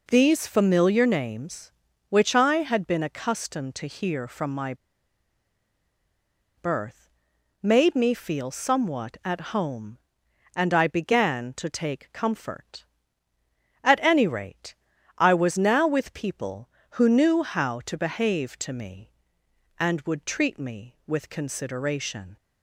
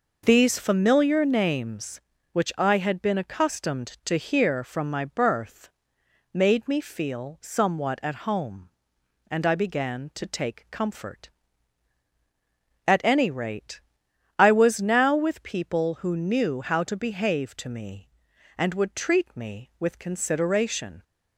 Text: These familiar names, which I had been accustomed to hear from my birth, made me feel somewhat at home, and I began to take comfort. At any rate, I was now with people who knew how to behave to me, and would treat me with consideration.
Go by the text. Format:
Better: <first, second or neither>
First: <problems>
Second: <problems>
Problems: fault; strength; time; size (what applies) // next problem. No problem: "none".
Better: second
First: pauses between "my" and "birth"; strong; at 4.7 s; 1.8 s long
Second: none